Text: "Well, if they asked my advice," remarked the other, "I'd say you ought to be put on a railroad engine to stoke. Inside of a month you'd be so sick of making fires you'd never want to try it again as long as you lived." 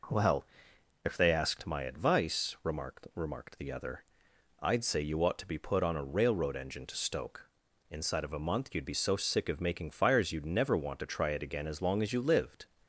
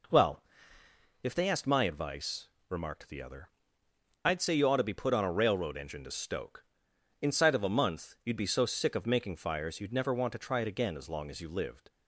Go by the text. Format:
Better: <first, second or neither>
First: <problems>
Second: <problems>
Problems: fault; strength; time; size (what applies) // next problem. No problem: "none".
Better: second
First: says "remarked" twice; at 3.1 s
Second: none